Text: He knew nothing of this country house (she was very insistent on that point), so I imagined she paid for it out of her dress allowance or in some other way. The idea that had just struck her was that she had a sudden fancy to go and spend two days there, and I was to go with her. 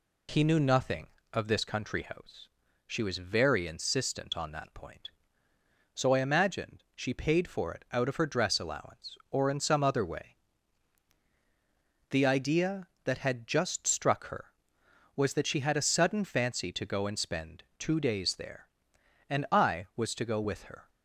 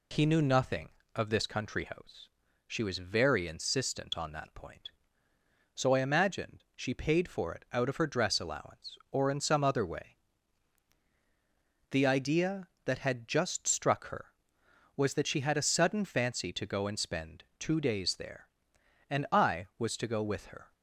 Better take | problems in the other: neither | pauses between "spend" and "two"; slight; the same in both

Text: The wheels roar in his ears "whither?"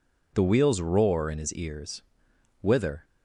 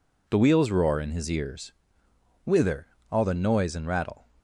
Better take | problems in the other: first | pauses between "ears" and "whither"; noticeable; at 1.7 s; 0.72 s long; noticeable in the first // goes on to say "All the noise and rattle"; noticeable; from 3.1 s on; 1.1 s long

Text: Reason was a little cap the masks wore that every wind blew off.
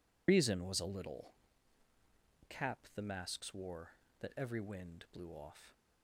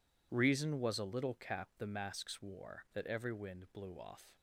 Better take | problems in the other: second | loses the start of "Reason"; at 0.2 s; 85 ms // pauses between "little" and "cap"; at 1.3 s; 1.1 s long

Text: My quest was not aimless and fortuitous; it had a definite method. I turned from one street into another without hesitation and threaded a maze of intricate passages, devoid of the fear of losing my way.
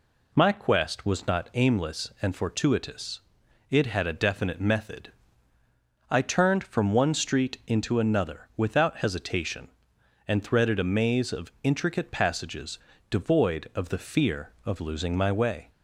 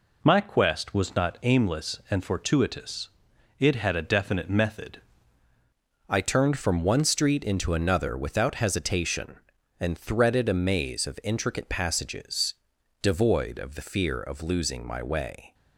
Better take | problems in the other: first | changes voice at "I"; from 6.0 s on; 9.5 s long

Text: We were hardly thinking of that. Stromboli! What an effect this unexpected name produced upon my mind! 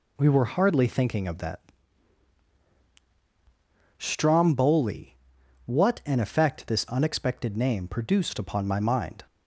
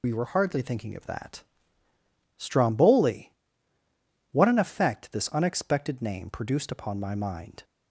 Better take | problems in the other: first | loses the start of "We"; at 0.0 s; 40 ms

